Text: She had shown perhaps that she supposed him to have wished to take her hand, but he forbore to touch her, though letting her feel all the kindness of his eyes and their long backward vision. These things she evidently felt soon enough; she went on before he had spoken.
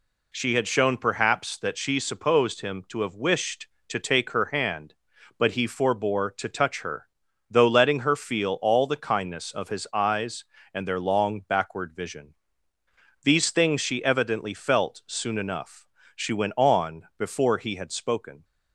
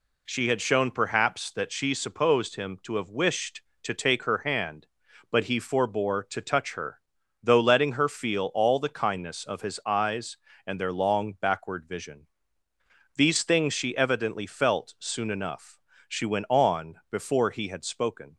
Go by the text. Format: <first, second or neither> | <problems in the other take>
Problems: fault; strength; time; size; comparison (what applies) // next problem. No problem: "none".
neither | pauses between "on" and "before"; slight; the same in both